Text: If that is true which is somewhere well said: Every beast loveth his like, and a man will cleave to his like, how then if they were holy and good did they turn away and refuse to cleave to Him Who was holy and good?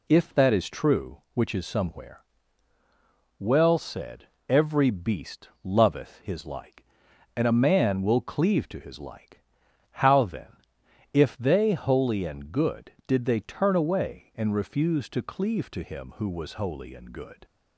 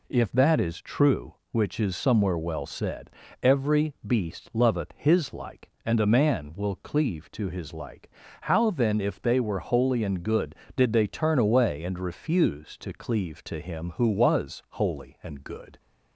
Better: second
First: pauses between "somewhere" and "well"; at 2.2 s; 1.1 s long // pauses between "beast" and "loveth"; slight; at 5.4 s; 0.16 s long // pauses between "then" and "if"; noticeable; at 10.5 s; 0.58 s long // skips "were"; at 11.7 s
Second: none

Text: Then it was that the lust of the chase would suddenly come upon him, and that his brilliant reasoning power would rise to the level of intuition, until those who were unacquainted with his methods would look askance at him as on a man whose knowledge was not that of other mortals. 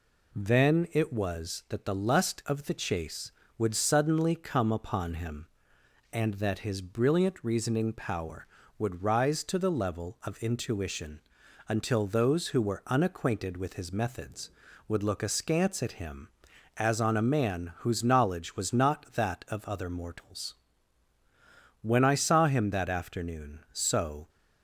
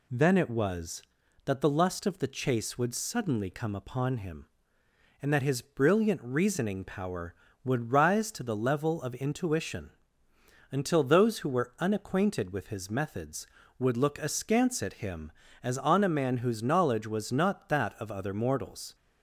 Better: second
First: goes on to say "When I saw him that afternoon so"; strong; from 21.8 s on; 2.4 s long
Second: none

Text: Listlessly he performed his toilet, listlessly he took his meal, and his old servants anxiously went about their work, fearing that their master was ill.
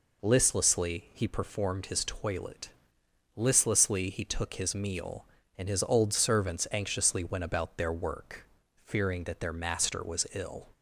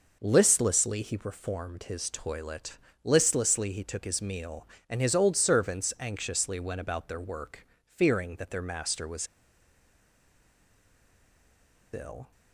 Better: first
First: none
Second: pauses between "was" and "ill"; strong; at 9.2 s; 2.6 s long

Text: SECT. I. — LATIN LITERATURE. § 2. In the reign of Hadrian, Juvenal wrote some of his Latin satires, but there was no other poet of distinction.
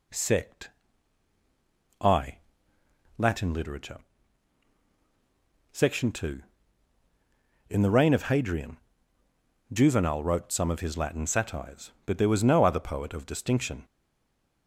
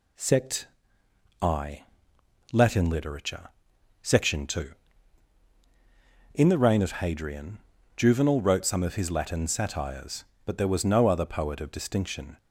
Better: second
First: stays silent after the last word; slight; from 13.8 s on; 0.8 s long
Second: none

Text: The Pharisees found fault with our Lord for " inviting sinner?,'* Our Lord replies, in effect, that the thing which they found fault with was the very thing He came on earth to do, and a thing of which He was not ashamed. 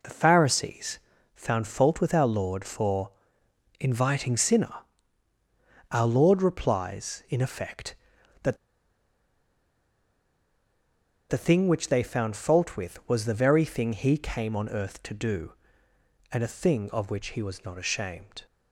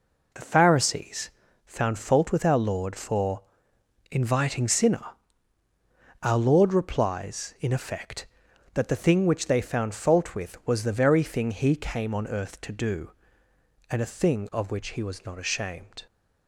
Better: second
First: pauses between "Pharisees" and "found"; slight; at 0.9 s; 0.36 s long // pauses between "that" and "the"; strong; at 8.5 s; 2.7 s long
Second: pauses between "Pharisees" and "found"; slight; at 1.2 s; 0.36 s long

